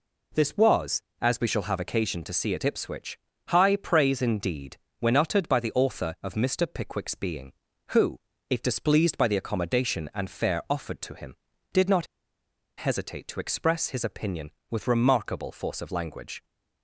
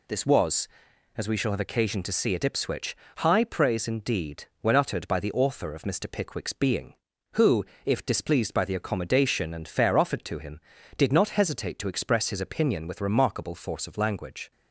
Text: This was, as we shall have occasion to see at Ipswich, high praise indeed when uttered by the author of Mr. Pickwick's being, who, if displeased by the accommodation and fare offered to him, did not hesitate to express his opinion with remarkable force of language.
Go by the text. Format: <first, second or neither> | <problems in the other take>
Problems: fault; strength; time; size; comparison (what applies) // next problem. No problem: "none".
second | pauses between "indeed" and "when"; slight; at 4.7 s; 0.22 s long; slight in the second // pauses between "not" and "hesitate"; noticeable; at 12.0 s; 0.72 s long